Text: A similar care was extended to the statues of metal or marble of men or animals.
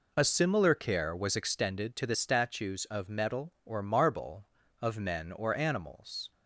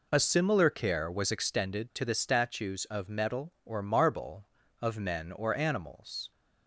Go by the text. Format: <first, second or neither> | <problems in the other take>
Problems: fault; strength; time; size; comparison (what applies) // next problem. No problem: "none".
neither | none